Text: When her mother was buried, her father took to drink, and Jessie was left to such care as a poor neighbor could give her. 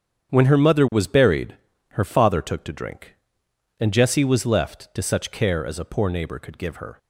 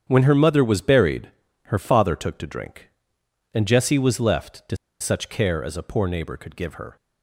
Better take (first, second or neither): first